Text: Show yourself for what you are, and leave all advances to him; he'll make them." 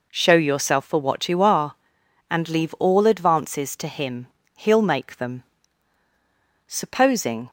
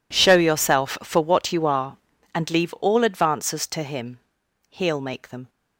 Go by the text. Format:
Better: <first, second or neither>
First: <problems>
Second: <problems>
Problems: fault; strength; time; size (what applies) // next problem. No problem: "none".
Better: second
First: goes on to say "Supposing"; noticeable; from 6.6 s on; 0.84 s long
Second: none